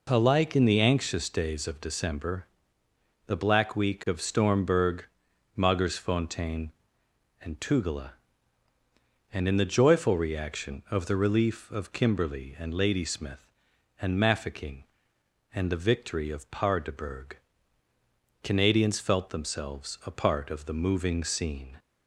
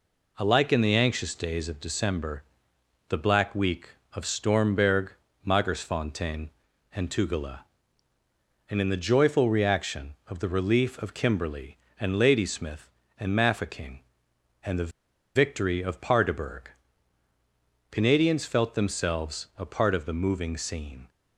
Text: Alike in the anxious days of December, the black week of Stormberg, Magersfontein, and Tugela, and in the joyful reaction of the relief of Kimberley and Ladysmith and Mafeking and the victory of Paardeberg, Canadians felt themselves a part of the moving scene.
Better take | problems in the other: first | pauses between "the" and "victory"; at 14.9 s; 0.44 s long

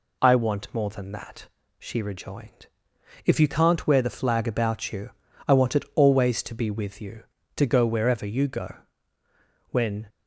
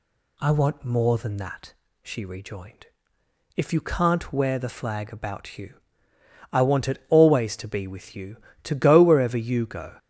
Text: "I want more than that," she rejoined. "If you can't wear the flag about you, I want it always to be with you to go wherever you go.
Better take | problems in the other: second | goes on to say "When"; slight; from 9.6 s on; 0.40 s long

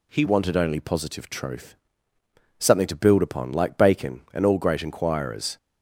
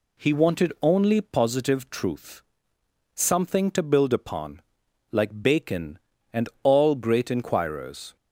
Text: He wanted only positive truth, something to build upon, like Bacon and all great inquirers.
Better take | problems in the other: second | changes voice at "wanted"; from 0.2 s on; 5.3 s long

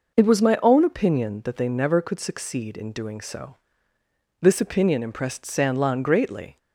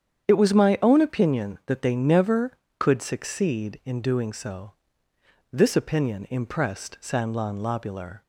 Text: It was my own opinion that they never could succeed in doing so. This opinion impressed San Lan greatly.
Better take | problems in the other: first | starts louder than the rest; strong; until 1.3 s; 8.5 dB // says "lobular" for "greatly"; at 7.5 s

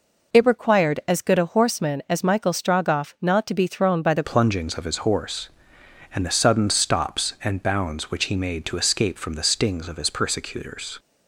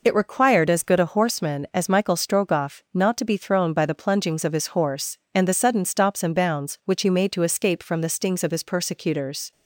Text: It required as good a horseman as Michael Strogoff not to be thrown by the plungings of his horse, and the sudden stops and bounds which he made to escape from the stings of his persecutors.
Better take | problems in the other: second | changes voice at "plungings"; from 4.2 s on; 6.7 s long

